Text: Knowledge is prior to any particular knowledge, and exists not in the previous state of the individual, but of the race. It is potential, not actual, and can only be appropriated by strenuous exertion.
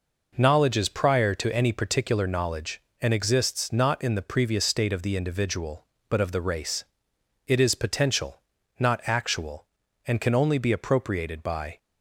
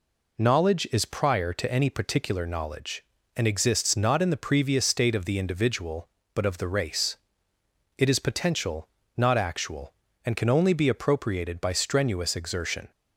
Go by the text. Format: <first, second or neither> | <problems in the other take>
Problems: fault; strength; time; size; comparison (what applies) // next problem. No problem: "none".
second | stops before "strenuous exertion"; at 11.7 s